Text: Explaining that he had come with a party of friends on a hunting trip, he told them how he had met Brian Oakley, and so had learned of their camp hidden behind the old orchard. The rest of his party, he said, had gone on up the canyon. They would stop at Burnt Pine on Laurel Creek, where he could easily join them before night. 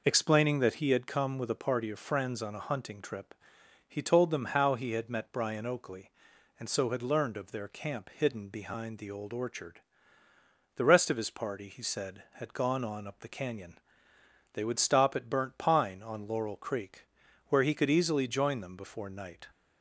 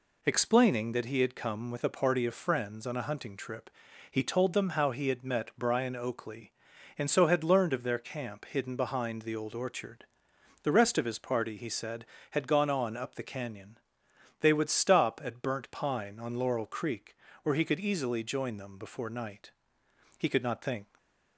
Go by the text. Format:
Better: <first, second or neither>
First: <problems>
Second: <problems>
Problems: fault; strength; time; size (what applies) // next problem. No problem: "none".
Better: first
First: none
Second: goes on to say "He could not think"; noticeable; from 20.1 s on; 0.78 s long // stays silent after the last word; slight; from 20.8 s on; 0.5 s long